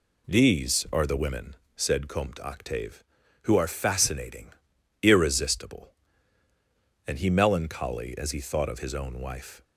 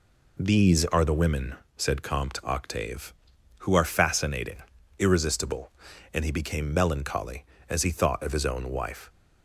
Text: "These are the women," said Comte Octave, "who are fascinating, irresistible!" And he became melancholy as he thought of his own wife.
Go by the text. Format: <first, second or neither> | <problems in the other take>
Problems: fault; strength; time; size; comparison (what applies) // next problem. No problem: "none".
second | skips "became"; at 7.2 s